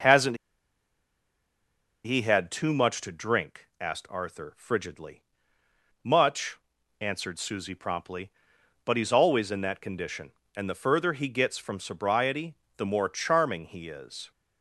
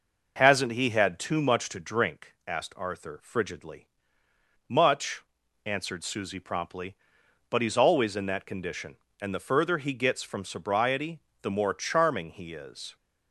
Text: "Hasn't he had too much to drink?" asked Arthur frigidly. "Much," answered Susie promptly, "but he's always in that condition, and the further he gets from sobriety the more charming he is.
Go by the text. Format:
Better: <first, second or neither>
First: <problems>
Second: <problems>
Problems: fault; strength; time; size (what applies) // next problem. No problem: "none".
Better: second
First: pauses between "Hasn't" and "he"; strong; at 0.3 s; 1.6 s long // pauses between "sobriety" and "the"; slight; at 12.5 s; 0.22 s long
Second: pauses between "sobriety" and "the"; slight; at 11.1 s; 0.22 s long